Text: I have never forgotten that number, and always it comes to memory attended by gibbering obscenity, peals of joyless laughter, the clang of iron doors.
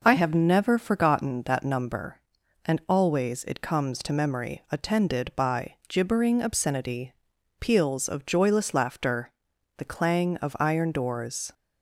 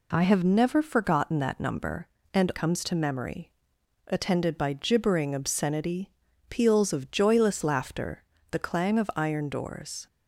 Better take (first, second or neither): first